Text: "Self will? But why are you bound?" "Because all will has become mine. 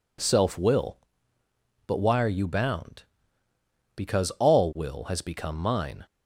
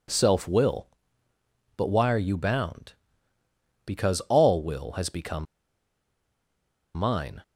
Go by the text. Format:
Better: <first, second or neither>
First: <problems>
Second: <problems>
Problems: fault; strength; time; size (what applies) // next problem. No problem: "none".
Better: first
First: none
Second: pauses between "become" and "mine"; strong; at 5.4 s; 1.5 s long